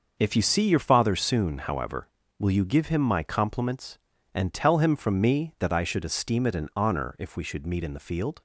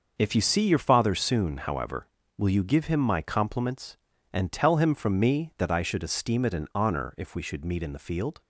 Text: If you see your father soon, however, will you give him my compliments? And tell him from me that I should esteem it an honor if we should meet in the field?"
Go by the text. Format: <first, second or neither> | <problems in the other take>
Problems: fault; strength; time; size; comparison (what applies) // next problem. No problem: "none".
neither | starts louder than the rest; noticeable; the same in both